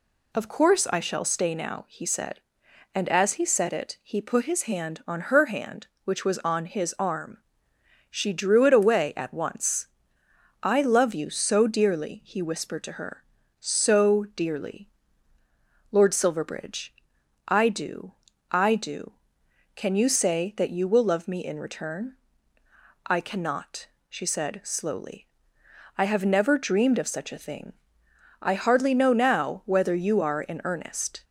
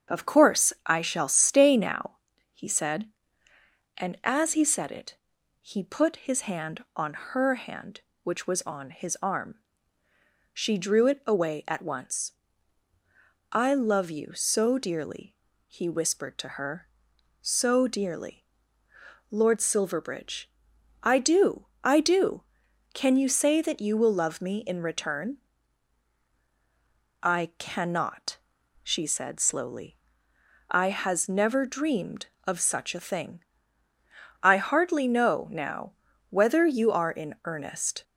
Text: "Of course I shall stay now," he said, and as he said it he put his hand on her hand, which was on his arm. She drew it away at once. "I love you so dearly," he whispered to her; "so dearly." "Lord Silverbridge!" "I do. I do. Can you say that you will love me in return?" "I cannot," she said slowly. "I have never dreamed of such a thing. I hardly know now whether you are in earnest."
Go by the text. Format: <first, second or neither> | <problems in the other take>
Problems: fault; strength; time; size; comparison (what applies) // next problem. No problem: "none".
first | starts louder than the rest; strong; until 1.2 s; 7.5 dB // pauses between "it" and "he"; noticeable; at 5.1 s; 0.46 s long // says "has" for "have"; at 30.8 s // pauses between "now" and "whether"; slight; at 35.9 s; 0.36 s long